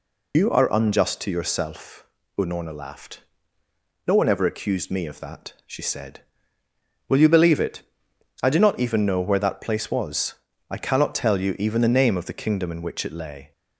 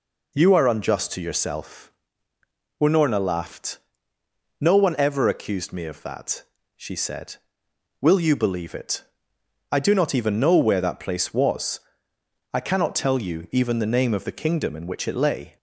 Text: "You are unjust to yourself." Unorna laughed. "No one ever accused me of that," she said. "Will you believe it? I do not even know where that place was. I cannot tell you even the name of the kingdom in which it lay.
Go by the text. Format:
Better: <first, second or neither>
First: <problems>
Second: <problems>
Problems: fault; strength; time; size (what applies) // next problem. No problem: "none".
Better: second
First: loses the start of "You"; at 0.3 s; 105 ms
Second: none